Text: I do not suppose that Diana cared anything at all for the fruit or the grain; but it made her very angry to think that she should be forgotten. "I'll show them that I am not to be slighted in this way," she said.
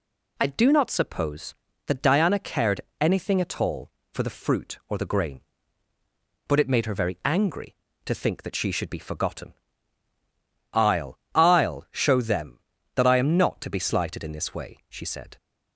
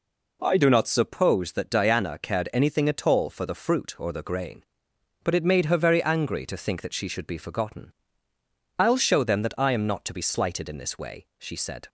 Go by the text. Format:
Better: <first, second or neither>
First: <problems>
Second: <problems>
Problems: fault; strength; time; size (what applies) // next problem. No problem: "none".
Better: second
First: pauses between "cared" and "anything"; slight; at 2.8 s; 0.20 s long // says "I'll" twice; at 11.3 s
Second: none